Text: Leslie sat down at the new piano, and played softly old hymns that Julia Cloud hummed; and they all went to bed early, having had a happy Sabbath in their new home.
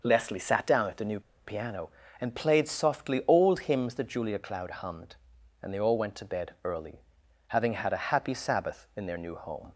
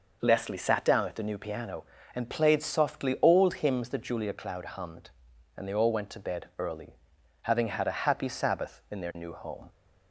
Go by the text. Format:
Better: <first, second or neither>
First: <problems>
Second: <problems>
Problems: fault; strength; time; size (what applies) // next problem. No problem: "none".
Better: second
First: pauses between "new" and "piano"; slight; at 1.1 s; 0.26 s long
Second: none